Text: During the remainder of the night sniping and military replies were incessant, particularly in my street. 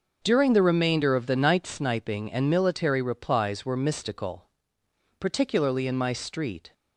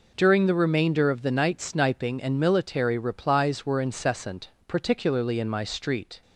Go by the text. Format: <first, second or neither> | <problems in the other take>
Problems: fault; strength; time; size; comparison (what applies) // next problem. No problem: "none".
second | says "mystical" for "incessant"; at 3.7 s